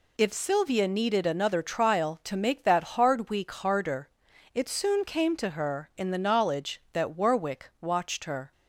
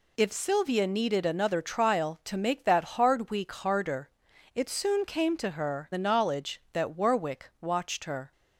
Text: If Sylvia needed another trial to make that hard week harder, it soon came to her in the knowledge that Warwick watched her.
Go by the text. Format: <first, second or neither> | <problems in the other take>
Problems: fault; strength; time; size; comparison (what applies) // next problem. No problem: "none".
first | skips "in"; at 5.9 s